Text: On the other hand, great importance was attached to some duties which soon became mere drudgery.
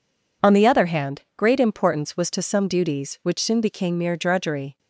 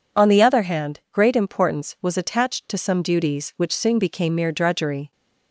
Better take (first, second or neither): second